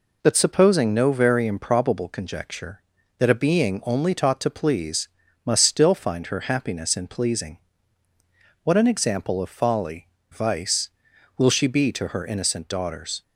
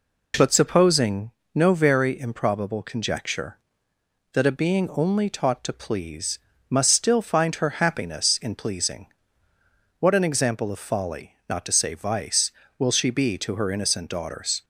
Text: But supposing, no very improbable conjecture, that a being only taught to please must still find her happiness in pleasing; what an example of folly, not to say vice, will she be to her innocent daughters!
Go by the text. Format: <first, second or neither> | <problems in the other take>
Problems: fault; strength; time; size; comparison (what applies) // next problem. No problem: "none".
second | pauses between "please" and "must"; at 5.0 s; 0.38 s long; slight in the second // skips "not to say"; at 10.1 s